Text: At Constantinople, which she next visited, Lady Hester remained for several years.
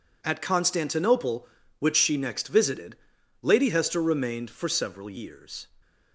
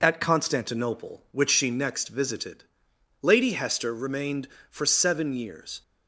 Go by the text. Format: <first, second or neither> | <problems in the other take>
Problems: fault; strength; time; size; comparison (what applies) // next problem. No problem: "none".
first | says "seven" for "several"; at 4.8 s